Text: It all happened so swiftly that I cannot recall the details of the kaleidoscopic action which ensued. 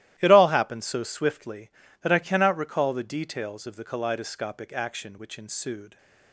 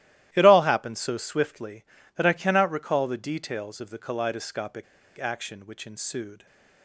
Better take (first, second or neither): first